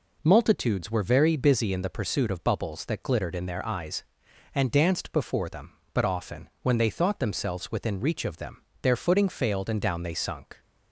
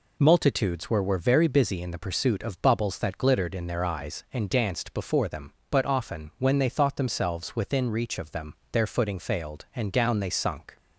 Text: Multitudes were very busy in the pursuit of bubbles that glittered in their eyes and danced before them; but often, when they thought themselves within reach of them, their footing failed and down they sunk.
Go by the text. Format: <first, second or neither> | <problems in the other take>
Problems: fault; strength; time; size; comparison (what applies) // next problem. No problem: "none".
first | says "were" twice; at 1.0 s